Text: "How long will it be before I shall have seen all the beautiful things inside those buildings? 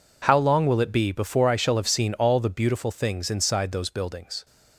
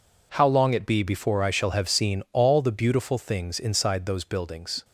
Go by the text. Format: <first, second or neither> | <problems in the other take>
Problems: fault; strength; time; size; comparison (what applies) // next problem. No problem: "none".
first | skips "will"; at 0.7 s